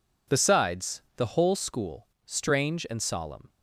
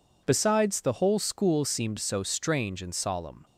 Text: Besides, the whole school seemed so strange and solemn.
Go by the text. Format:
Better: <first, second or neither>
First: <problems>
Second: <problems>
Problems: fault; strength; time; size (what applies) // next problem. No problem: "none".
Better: second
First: skips "seemed so"; at 2.1 s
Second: none